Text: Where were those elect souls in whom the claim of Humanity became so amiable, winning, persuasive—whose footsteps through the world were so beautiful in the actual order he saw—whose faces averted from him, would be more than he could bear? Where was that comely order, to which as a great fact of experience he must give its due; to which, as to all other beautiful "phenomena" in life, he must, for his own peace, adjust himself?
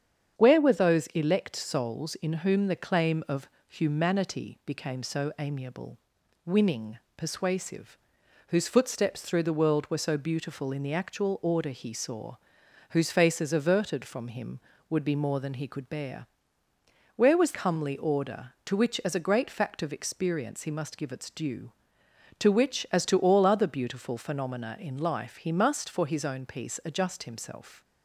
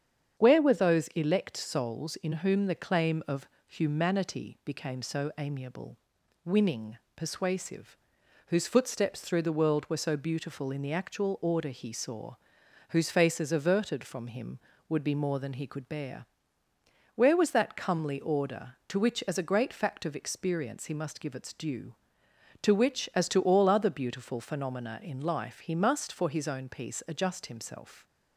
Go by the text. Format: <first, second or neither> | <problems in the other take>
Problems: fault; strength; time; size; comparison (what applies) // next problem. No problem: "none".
second | starts louder than the rest; strong; until 1.4 s; 8 dB; strong in the second // pauses between "of" and "Humanity"; slight; at 3.4 s; 0.20 s long; slight in the second // skips "that"; at 17.5 s